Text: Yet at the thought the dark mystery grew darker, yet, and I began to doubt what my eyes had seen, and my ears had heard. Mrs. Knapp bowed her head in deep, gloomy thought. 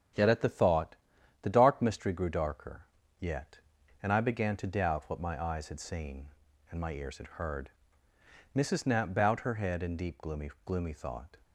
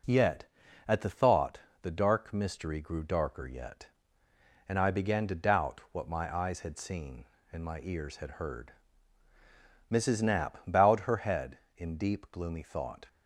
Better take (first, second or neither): second